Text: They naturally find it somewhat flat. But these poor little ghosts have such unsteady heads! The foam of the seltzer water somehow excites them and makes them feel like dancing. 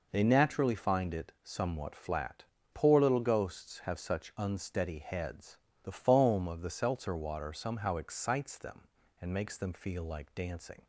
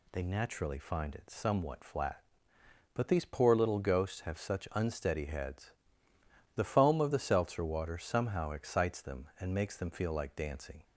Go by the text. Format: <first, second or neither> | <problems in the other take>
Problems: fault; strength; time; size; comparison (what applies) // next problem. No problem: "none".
second | skips "But these"; at 2.5 s